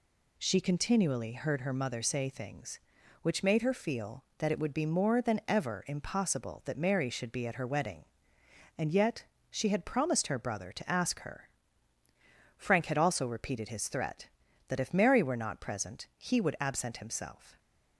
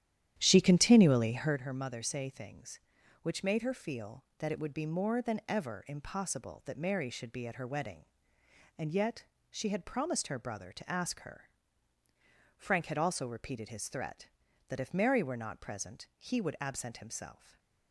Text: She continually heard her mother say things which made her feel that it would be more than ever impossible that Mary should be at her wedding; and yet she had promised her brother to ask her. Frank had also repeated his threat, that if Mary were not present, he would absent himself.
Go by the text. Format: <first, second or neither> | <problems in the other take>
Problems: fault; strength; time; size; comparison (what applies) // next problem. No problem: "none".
first | starts louder than the rest; strong; until 1.6 s; 10.5 dB // pauses between "yet" and "she"; slight; at 9.2 s; 0.26 s long; slight in the first // stays silent after the last word; slight; from 17.3 s on; 0.6 s long